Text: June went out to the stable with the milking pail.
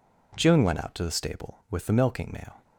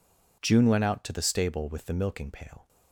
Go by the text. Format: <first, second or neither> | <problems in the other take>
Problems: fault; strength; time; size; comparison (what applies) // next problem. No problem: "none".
second | says "mail" for "pail"; at 2.3 s